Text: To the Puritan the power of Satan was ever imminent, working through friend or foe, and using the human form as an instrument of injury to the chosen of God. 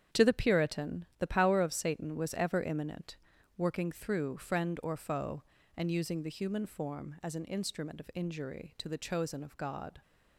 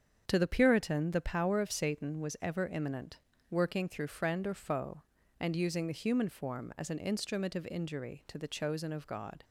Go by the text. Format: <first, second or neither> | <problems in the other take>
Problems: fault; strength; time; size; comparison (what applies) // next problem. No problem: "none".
neither | starts louder than the rest; strong; the same in both